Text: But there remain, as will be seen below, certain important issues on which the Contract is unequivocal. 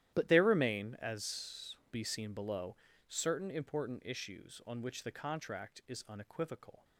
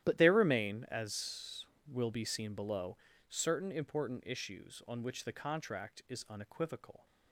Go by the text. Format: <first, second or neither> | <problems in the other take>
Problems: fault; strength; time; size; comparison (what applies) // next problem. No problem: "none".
second | starts louder than the rest; strong; until 1.1 s; 12 dB; strong in the second // skips "will"; at 1.8 s